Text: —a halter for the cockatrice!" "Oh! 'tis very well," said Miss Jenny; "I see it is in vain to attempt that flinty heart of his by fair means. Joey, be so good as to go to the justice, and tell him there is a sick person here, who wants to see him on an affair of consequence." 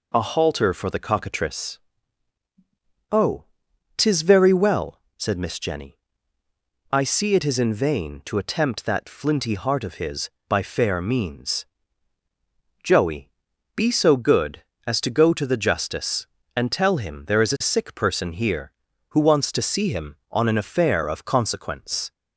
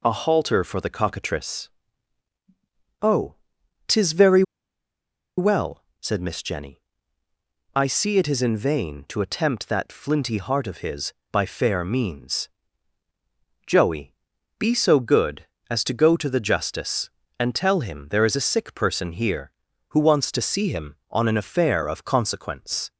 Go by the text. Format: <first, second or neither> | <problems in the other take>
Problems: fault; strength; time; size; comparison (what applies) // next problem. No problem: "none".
first | pauses between "very" and "well"; noticeable; at 4.4 s; 0.95 s long